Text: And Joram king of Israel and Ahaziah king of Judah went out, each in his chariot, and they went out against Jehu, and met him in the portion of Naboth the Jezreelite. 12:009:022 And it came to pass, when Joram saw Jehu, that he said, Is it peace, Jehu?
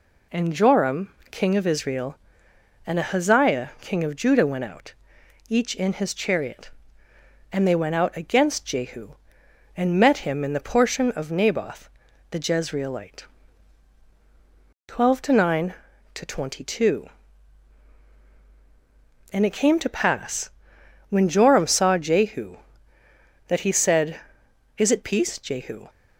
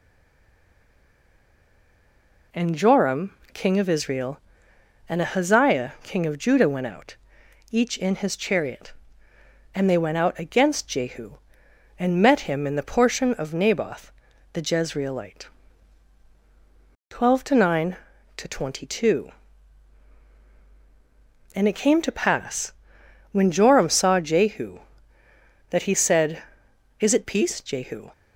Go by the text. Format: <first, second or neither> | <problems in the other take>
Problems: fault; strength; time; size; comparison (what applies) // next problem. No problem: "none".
first | stays silent before the first word; until 2.5 s; 2.5 s long // pauses between "Joram" and "king"; slight; at 3.3 s; 0.20 s long; slight in the first // pauses between "Naboth" and "the"; at 14.1 s; 0.42 s long; also in the first